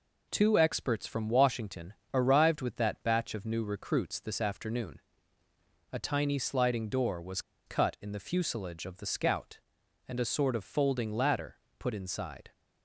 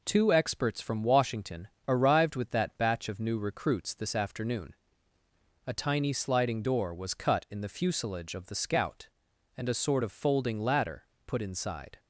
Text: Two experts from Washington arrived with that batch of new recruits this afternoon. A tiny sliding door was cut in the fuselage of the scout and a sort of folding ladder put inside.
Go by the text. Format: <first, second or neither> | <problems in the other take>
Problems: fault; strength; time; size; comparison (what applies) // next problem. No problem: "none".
second | pauses between "Washington" and "arrived"; slight; at 1.9 s; 0.18 s long; slight in the second // pauses between "was" and "cut"; slight; at 7.3 s; 0.26 s long // pauses between "ladder" and "put"; slight; at 11.5 s; 0.24 s long; slight in the second